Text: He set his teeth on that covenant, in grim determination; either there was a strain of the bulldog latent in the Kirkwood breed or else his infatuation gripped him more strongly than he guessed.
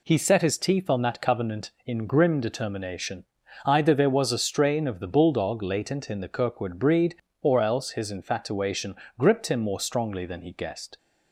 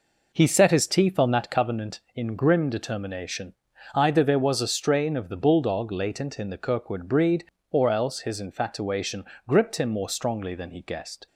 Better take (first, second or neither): first